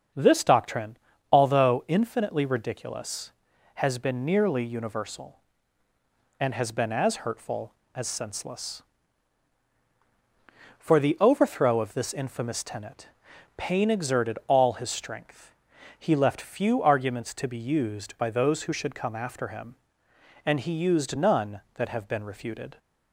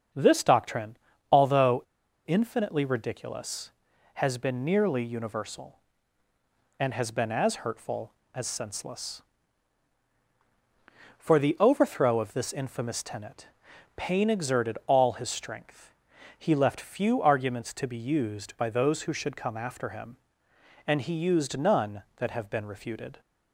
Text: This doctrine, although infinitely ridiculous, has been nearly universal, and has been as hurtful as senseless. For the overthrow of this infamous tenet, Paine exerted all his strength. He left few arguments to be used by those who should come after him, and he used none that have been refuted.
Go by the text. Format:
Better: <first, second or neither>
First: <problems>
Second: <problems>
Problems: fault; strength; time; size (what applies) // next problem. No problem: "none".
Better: first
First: starts louder than the rest; until 1.4 s; 6.5 dB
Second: starts louder than the rest; until 1.4 s; 6.5 dB // pauses between "although" and "infinitely"; at 1.8 s; 0.41 s long